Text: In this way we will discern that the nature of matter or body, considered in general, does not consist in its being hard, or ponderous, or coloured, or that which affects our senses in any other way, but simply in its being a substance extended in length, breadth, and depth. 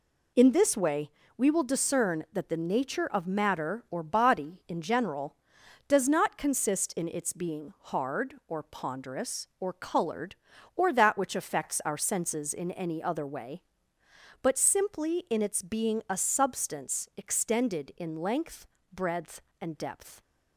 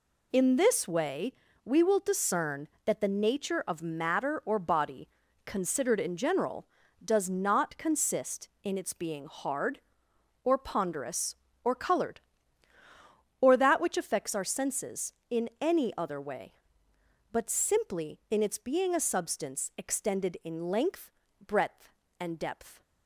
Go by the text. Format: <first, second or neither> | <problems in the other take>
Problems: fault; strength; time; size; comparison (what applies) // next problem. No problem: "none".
second | pauses between "way" and "we"; slight; at 1.0 s; 0.28 s long; slight in the second // skips "considered"; at 4.6 s